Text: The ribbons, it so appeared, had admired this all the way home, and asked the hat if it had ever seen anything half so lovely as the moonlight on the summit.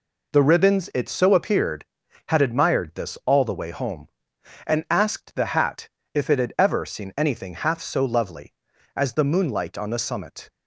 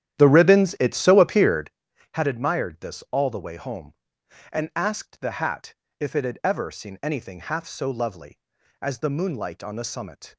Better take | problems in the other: first | starts louder than the rest; strong; until 1.8 s; 11.5 dB // pauses between "hat" and "if"; slight; at 5.7 s; 0.24 s long; slight in the first

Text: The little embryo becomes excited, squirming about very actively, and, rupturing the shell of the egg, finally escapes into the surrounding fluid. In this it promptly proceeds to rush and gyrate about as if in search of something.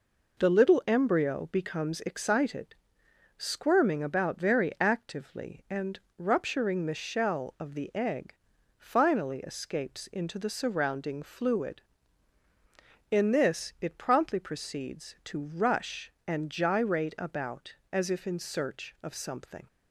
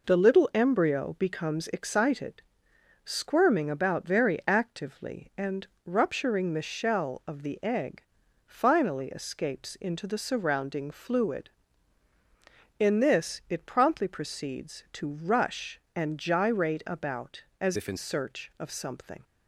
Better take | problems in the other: first | changes voice from "if" to "in"; from 17.7 to 17.9 s; 0.2 s long

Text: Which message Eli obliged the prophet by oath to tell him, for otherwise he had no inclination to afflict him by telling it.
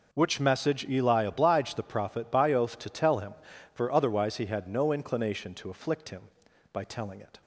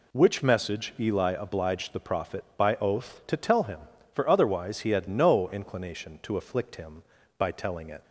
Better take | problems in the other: neither | none

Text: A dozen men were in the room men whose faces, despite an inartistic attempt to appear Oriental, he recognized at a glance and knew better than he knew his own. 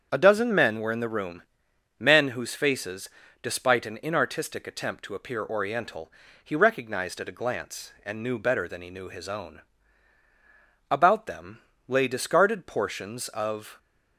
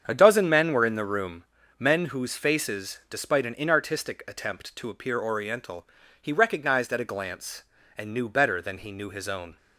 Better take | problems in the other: second | starts louder than the rest; strong; until 1.1 s; 7.5 dB; strong in the second // pauses between "room" and "men"; noticeable; at 1.4 s; 0.56 s long; slight in the second // goes on to say "About them lay discarded portions of"; strong; from 10.8 s on; 2.8 s long

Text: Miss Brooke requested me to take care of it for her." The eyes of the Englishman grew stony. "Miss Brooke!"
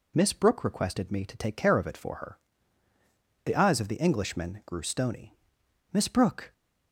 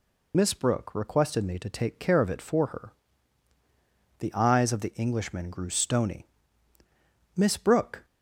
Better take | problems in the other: first | loses the start of "Miss"; at 0.3 s; 45 ms

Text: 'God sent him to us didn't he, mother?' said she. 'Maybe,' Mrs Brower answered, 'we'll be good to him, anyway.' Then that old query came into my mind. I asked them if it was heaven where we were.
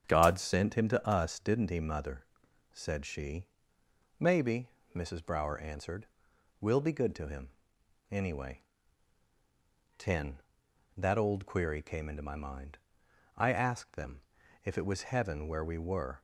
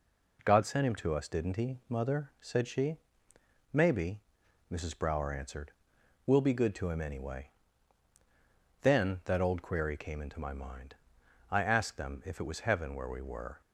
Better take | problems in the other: second | starts louder than the rest; strong; until 1.0 s; 8 dB // says "Ten" for "Then"; at 9.9 s // pauses between "them" and "if"; at 14.2 s; 0.42 s long

